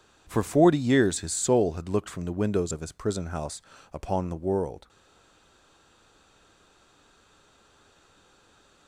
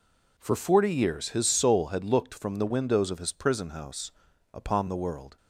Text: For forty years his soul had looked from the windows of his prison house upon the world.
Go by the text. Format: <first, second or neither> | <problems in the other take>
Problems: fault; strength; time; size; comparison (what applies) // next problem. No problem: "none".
second | pauses between "house" and "upon"; slight; at 3.6 s; 0.32 s long; also in the second // stays silent after the last word; strong; from 4.8 s on; 4.0 s long